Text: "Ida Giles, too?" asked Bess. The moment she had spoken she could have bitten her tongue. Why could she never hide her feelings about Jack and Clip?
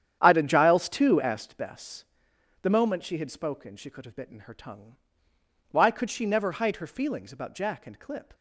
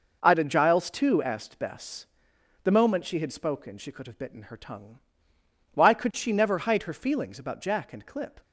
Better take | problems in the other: second | starts louder than the rest; strong; until 1.6 s; 9.5 dB

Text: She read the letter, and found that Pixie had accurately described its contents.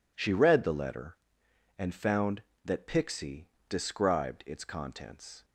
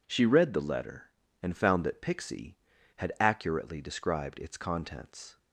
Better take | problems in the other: second | skips "had accurately"; at 3.5 s

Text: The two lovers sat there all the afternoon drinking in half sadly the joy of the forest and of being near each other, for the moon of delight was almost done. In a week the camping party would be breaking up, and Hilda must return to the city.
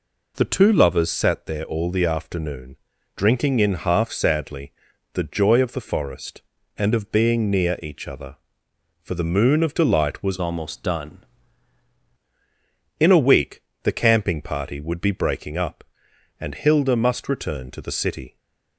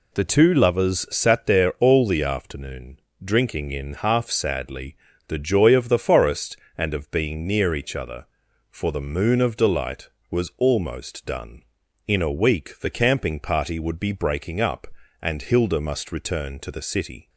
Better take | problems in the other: second | pauses between "afternoon" and "drinking"; at 2.7 s; 0.40 s long; slight in the second // pauses between "sadly" and "the"; at 4.7 s; 0.40 s long; slight in the second // changes voice from "almost" to "done"; from 10.3 to 11.2 s; 0.9 s long // pauses between "week" and "the"; slight; at 13.6 s; 0.22 s long

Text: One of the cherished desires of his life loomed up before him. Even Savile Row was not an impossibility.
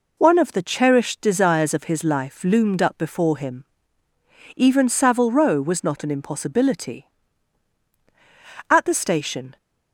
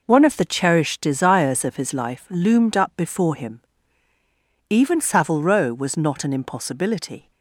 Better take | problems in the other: second | goes on to say "At the station"; noticeable; from 8.6 s on; 0.88 s long

